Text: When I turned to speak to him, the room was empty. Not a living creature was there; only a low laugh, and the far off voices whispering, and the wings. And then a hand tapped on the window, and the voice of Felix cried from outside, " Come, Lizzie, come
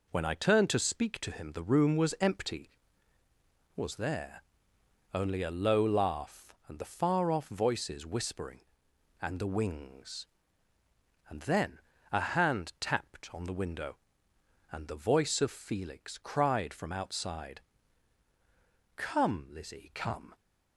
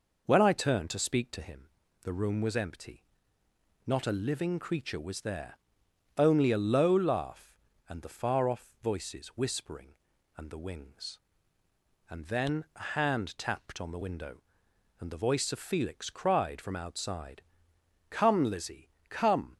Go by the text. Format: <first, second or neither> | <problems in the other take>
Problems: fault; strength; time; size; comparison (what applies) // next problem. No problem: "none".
second | skips "Not a living creature"; at 3.2 s // pauses between "then" and "a"; slight; at 11.7 s; 0.30 s long